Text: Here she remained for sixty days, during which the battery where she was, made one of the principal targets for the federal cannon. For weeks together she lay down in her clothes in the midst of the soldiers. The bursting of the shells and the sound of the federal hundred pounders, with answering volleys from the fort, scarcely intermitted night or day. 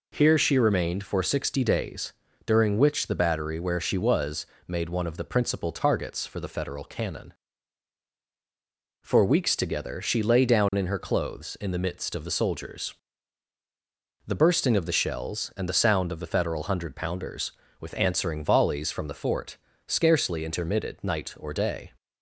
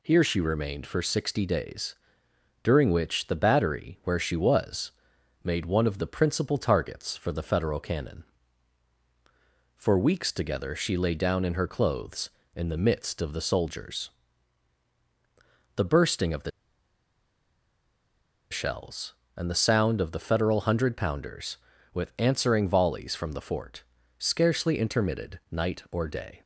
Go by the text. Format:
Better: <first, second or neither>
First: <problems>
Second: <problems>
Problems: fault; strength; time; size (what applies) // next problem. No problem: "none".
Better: first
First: none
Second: pauses between "the" and "shells"; strong; at 16.5 s; 2.0 s long